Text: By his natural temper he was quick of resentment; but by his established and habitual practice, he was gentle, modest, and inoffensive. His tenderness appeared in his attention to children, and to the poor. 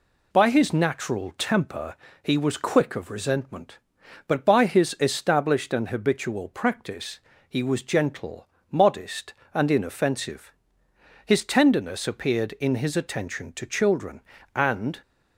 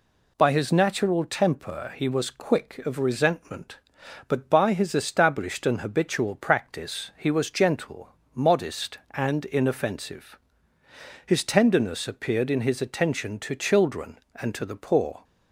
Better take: second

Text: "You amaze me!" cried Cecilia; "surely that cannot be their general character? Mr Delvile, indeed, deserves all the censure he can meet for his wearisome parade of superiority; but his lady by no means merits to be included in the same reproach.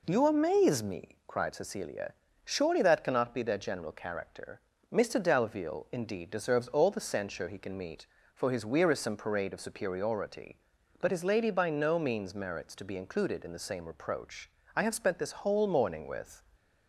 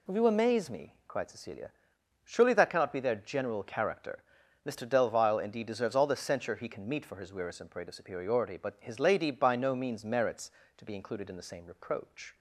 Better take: second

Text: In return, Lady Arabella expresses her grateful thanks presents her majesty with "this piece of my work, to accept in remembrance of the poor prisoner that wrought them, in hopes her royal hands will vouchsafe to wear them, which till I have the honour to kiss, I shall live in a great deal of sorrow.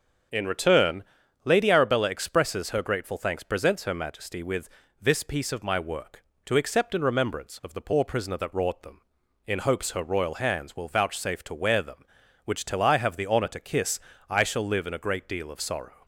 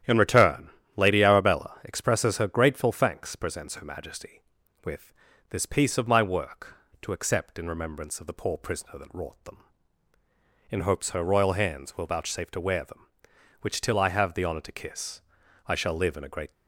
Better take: first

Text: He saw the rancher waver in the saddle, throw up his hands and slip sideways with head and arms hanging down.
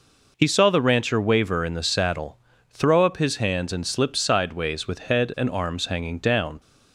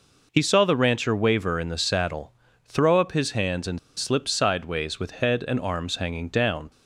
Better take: first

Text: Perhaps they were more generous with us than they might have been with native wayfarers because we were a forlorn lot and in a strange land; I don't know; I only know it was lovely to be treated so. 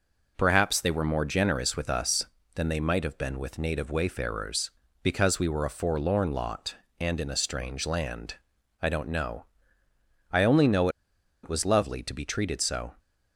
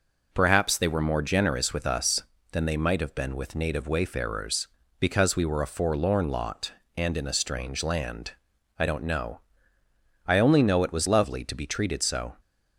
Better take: second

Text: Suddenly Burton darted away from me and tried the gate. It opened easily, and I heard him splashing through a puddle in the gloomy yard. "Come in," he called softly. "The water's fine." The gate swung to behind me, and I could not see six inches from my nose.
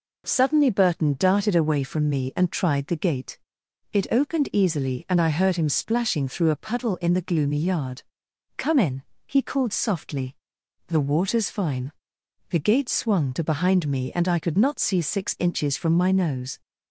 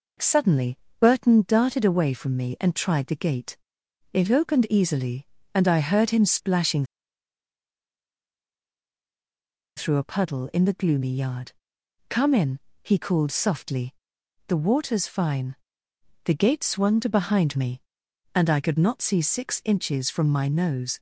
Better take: first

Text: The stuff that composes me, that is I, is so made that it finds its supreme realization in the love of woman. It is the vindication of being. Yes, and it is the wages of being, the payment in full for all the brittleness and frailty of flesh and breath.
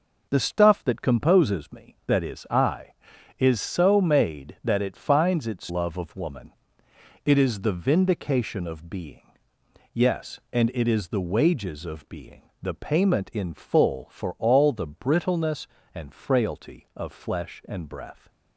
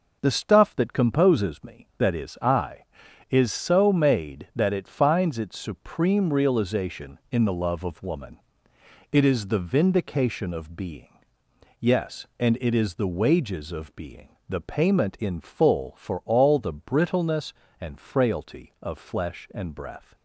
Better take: second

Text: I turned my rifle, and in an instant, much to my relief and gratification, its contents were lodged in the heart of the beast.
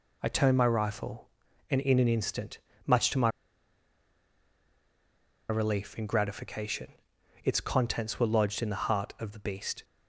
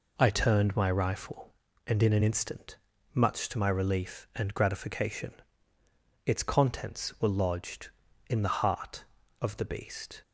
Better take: second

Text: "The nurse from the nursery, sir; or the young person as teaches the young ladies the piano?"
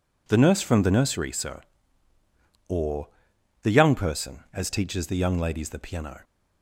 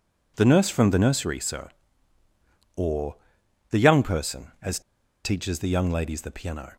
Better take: first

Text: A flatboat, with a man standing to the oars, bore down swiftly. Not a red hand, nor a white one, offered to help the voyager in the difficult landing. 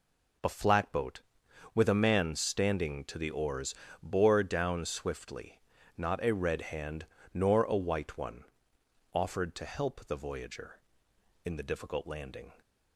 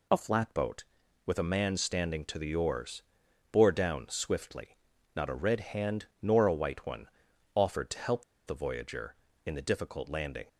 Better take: first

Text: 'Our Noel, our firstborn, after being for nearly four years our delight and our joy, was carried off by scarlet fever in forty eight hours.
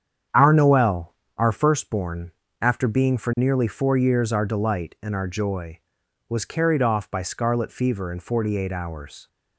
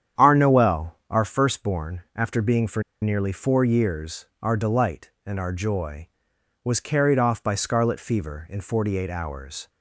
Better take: first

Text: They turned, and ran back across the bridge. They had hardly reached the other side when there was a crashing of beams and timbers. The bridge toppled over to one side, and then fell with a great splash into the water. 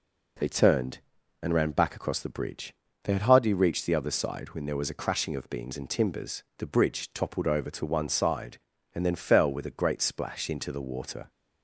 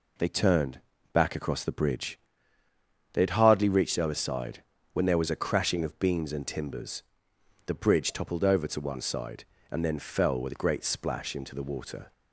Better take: first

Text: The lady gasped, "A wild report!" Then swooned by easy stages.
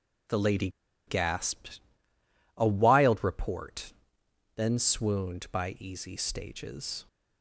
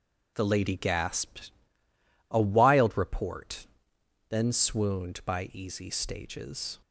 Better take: second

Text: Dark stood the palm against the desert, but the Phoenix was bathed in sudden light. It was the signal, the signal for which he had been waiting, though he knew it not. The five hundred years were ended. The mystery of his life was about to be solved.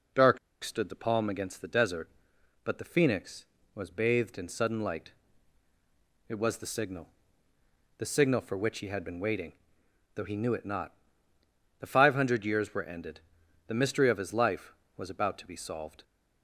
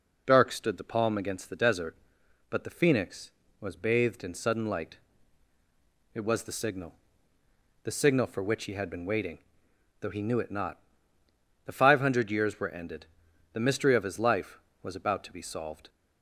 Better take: second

